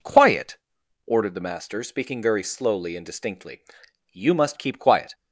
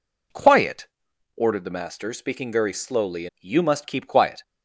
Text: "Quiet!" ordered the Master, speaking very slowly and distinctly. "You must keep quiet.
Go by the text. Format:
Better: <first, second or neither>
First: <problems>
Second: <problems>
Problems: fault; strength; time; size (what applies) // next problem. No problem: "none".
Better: first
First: none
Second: skips "and distinctly"; at 3.3 s